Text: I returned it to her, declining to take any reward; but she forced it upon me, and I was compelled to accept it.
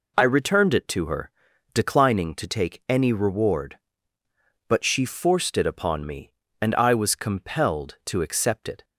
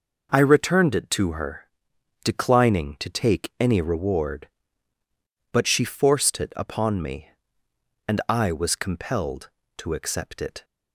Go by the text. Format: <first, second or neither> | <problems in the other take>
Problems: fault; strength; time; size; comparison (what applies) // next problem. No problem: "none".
neither | none